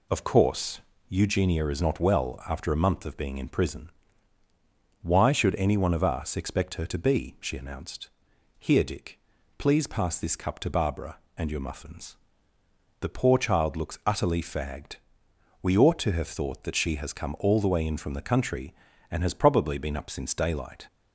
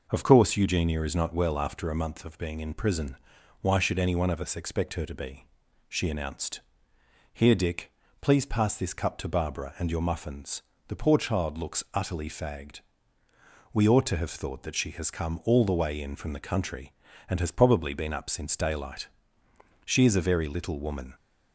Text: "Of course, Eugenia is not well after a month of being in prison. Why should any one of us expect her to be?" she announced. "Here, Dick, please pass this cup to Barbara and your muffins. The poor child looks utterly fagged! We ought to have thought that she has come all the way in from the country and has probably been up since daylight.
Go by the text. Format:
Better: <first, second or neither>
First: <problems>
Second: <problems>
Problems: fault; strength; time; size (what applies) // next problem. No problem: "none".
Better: first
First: none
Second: goes on to say "She is a very little woman"; noticeable; from 19.8 s on; 1.3 s long